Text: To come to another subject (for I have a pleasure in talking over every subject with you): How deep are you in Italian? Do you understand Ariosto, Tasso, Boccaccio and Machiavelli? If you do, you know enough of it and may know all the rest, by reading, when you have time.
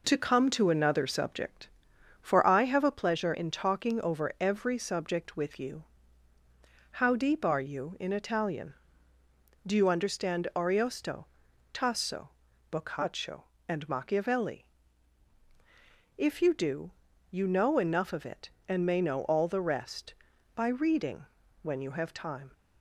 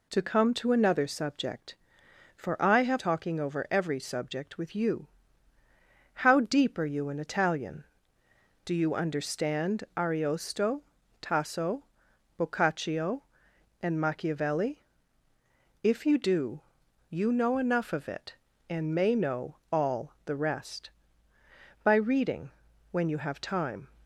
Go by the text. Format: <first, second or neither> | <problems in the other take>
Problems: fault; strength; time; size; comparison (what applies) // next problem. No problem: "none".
first | skips "a pleasure in"; at 2.9 s // pauses between "know" and "all"; slight; at 19.5 s; 0.16 s long